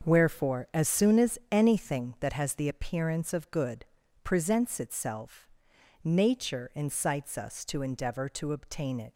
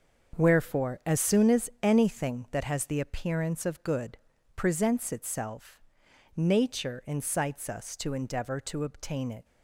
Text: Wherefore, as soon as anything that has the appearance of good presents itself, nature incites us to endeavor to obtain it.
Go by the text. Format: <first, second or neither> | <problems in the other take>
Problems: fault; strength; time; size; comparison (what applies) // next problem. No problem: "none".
neither | starts louder than the rest; the same in both // pauses between "good" and "presents"; the same in both